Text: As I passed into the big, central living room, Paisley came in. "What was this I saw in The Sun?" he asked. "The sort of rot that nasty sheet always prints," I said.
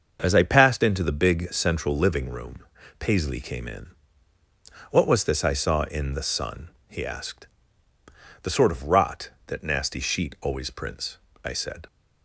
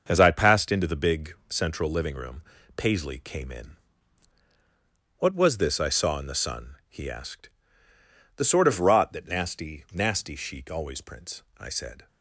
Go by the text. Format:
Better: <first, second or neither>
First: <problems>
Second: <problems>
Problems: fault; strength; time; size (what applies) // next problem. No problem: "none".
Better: first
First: starts louder than the rest; until 1.2 s; 6.5 dB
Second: starts louder than the rest; until 1.0 s; 6.5 dB // says "nasty" twice; at 9.9 s